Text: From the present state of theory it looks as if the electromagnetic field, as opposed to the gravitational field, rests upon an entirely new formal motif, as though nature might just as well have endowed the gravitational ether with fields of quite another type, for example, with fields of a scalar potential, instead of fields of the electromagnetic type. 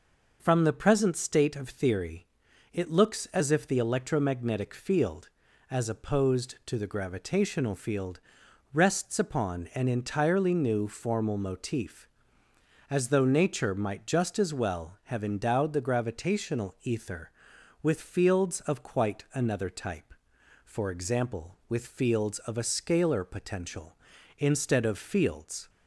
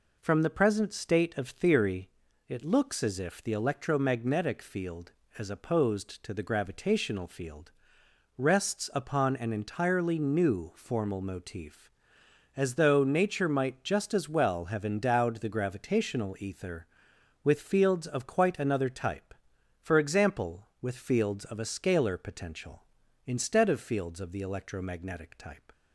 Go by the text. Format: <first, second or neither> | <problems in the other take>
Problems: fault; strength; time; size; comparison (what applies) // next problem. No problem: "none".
second | pauses between "theory" and "it"; noticeable; at 2.2 s; 0.48 s long; also in the second // stops before "of the electromagnetic type"; at 25.6 s